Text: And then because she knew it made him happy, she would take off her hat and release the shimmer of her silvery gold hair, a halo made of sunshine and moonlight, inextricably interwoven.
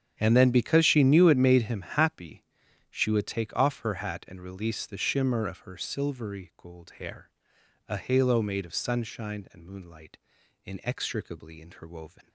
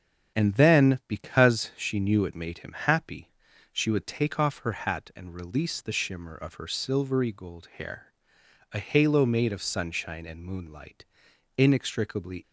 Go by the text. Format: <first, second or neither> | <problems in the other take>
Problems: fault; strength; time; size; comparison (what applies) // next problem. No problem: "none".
first | starts louder than the rest; strong; until 1.4 s; 8.5 dB; strong in the first // stops before "interwoven"; at 12.4 s